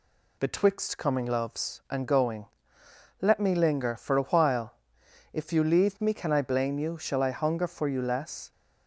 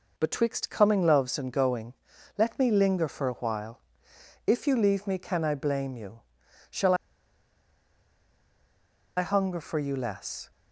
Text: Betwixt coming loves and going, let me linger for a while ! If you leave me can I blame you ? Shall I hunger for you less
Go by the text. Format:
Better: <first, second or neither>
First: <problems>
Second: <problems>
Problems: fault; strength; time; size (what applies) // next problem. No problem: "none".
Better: first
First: none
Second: pauses between "Shall" and "I"; strong; at 6.9 s; 2.2 s long